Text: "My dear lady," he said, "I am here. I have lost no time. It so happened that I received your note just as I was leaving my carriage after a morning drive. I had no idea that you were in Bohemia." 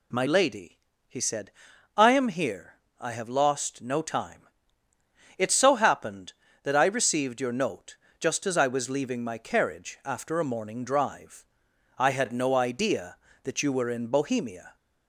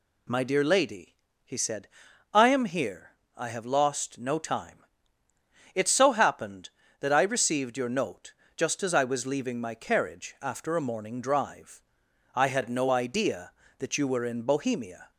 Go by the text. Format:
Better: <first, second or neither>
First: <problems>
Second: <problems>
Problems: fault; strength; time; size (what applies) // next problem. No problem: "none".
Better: second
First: skips "dear"; at 0.2 s // pauses between "note" and "just"; slight; at 7.9 s; 0.20 s long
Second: pauses between "note" and "just"; slight; at 8.3 s; 0.20 s long